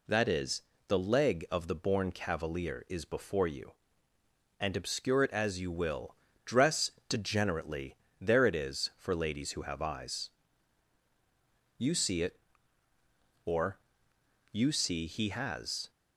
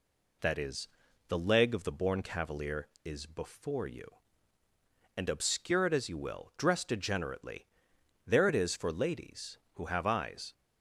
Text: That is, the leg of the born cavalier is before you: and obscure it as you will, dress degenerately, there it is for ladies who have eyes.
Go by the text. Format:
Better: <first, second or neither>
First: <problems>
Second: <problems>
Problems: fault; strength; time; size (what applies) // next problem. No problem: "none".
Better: second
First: pauses between "dress" and "degenerately"; slight; at 6.8 s; 0.18 s long // goes on to say "You see it or you see he has"; strong; from 11.7 s on; 4.1 s long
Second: none